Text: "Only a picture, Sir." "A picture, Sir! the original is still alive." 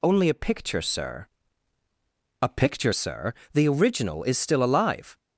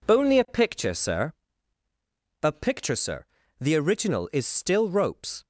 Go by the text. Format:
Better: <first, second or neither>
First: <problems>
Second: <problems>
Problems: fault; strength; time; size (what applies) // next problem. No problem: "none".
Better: first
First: none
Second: says "ropes" for "alive"; at 4.8 s